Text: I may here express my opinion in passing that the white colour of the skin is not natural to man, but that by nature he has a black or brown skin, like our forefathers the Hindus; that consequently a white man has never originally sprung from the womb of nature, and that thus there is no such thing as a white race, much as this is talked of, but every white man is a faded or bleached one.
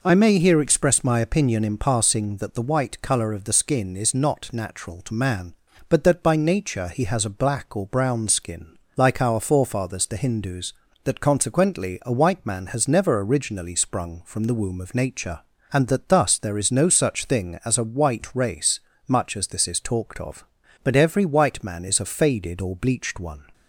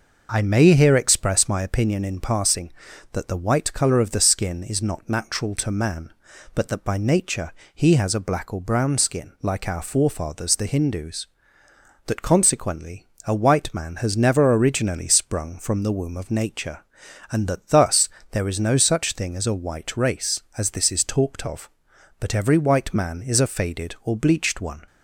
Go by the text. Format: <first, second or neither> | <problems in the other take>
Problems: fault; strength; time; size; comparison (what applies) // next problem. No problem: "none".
first | pauses between "nature" and "he"; slight; at 7.5 s; 0.22 s long // pauses between "consequently" and "a"; slight; at 13.0 s; 0.20 s long // pauses between "thus" and "there"; slight; at 18.0 s; 0.22 s long // skips "much"; at 20.4 s